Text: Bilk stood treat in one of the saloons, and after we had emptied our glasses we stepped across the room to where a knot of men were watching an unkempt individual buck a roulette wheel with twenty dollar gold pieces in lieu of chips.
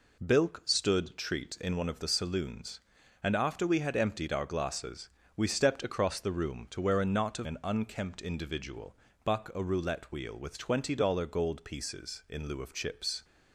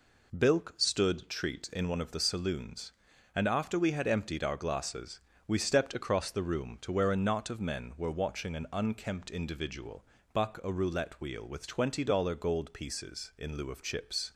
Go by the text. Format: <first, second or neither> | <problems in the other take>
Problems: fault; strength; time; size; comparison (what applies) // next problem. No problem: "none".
second | pauses between "glasses" and "we"; slight; at 5.0 s; 0.26 s long; slight in the second // skips "men were watching"; at 7.4 s // pauses between "individual" and "buck"; slight; at 8.9 s; 0.30 s long; slight in the second